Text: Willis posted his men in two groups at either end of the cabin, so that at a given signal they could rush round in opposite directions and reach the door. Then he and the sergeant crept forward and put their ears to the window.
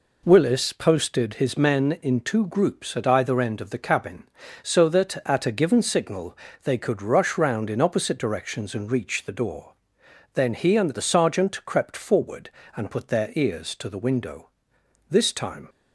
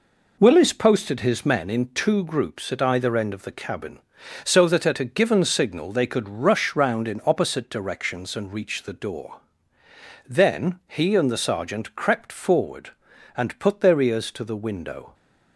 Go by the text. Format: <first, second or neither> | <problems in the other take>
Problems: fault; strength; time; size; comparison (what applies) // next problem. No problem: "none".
second | pauses between "signal" and "they"; slight; at 6.3 s; 0.26 s long // goes on to say "This time"; from 15.0 s on; 0.60 s long